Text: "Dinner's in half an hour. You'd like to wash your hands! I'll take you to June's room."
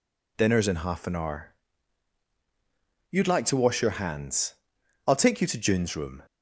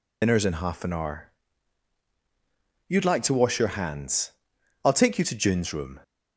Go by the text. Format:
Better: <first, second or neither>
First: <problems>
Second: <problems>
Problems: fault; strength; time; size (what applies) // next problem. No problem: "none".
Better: first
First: none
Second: loses the start of "Dinner's"; at 0.2 s; 75 ms